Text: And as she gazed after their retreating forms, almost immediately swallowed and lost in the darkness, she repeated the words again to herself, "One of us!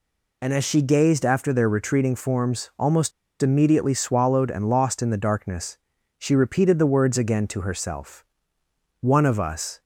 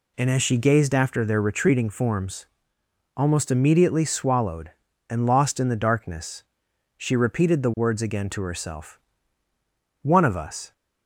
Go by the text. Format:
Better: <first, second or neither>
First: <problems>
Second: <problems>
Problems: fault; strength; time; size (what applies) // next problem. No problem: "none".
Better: second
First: pauses between "almost" and "immediately"; slight; at 3.1 s; 0.31 s long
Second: none